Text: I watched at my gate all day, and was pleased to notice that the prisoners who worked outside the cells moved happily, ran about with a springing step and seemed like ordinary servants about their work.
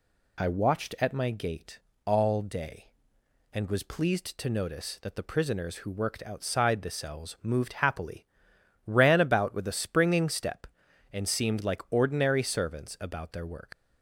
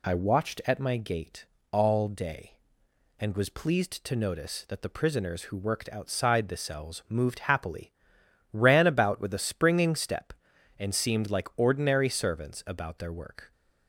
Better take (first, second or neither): second